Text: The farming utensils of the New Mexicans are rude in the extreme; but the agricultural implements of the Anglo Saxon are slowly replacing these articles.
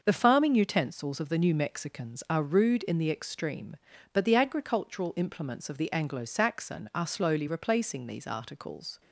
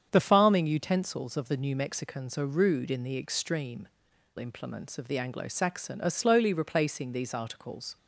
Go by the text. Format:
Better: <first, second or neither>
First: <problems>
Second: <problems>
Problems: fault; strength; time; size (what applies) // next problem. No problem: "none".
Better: first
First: starts louder than the rest; noticeable; until 1.0 s; 6 dB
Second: starts louder than the rest; strong; until 1.1 s; 8 dB // skips "but the agricultural"; at 4.1 s